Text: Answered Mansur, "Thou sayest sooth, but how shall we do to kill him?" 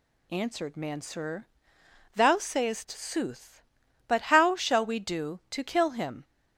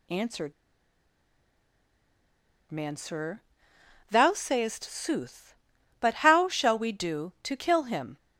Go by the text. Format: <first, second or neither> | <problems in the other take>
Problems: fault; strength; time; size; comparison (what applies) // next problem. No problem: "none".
first | pauses between "Answered" and "Mansur"; strong; at 0.5 s; 2.1 s long